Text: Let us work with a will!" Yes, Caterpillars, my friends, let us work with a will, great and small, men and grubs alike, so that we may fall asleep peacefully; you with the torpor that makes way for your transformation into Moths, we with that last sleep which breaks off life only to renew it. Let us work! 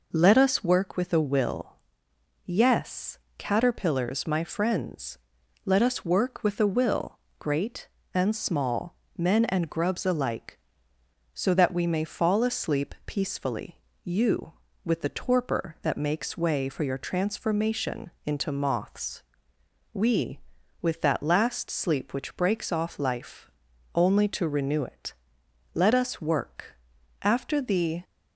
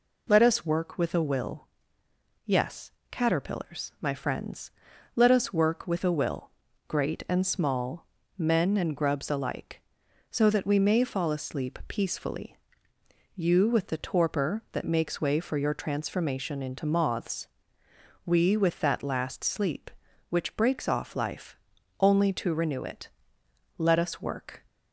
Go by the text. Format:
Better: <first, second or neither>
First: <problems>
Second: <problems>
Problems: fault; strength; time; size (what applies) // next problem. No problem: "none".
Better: second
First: pauses between "transformation" and "into"; slight; at 18.0 s; 0.16 s long // pauses between "life" and "only"; noticeable; at 23.4 s; 0.46 s long // goes on to say "After the"; noticeable; from 27.2 s on; 0.80 s long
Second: pauses between "life" and "only"; at 21.5 s; 0.44 s long